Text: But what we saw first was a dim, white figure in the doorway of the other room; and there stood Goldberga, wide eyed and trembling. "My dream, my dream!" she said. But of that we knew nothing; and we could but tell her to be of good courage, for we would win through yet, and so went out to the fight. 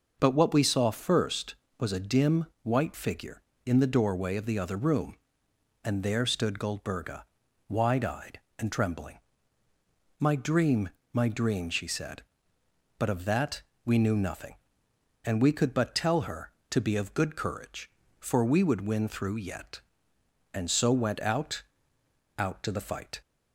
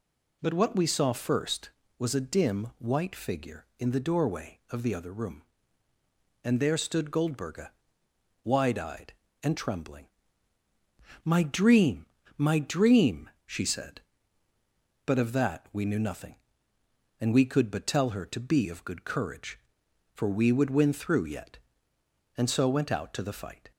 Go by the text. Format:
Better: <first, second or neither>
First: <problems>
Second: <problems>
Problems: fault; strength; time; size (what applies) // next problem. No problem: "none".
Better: second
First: pauses between "that" and "we"; slight; at 13.6 s; 0.24 s long // says "out" twice; at 22.3 s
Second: none